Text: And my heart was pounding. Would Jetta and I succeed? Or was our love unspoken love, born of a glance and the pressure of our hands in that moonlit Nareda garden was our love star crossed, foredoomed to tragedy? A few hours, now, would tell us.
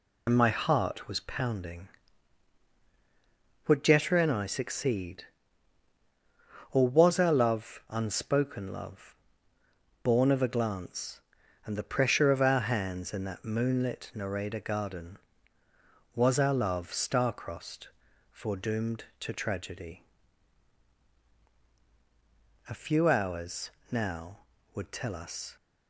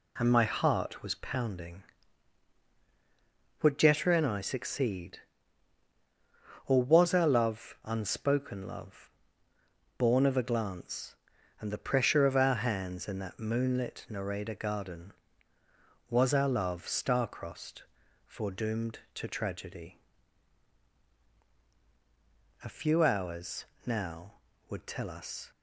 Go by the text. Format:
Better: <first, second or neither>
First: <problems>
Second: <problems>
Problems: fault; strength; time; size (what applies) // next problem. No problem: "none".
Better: second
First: loses the start of "And"; at 0.2 s; 65 ms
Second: none